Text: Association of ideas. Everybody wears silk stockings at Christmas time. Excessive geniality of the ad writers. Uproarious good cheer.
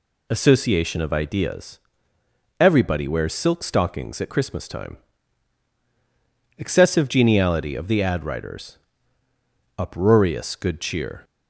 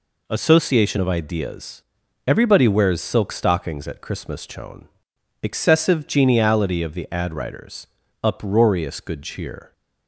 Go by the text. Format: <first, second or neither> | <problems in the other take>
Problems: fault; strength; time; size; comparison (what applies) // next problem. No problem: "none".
first | says "chone" for "time"; at 4.4 s